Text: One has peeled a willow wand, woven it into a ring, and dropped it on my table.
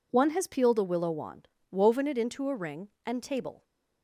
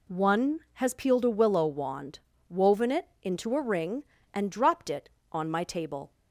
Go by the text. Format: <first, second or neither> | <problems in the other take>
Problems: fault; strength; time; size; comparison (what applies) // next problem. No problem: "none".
second | skips "dropped it on my"; at 3.2 s